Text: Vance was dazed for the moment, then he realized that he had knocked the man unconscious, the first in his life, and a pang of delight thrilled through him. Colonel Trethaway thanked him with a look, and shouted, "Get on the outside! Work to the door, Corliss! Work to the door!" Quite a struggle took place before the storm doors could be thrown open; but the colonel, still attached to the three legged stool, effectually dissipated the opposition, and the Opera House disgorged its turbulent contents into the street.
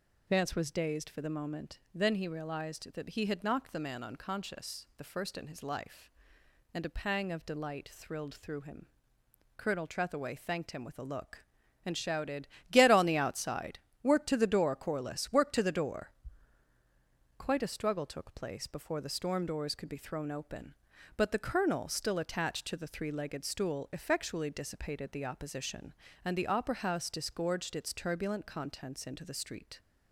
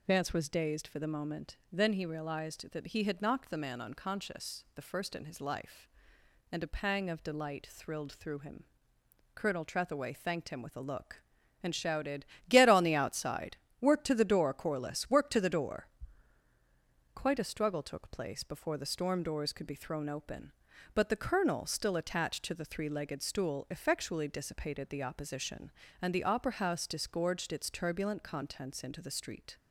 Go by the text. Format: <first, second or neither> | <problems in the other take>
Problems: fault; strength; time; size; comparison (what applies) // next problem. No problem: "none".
neither | none